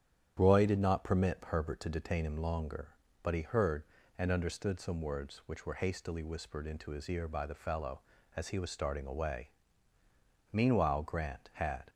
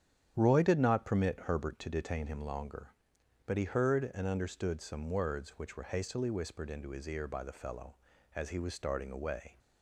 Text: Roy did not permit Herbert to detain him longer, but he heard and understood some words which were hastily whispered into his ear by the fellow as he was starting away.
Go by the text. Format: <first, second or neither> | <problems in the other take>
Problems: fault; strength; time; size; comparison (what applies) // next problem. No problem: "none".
second | starts louder than the rest; strong; until 1.3 s; 9.5 dB; strong in the second // goes on to say "Meanwhile Grant had"; from 10.5 s on; 1.3 s long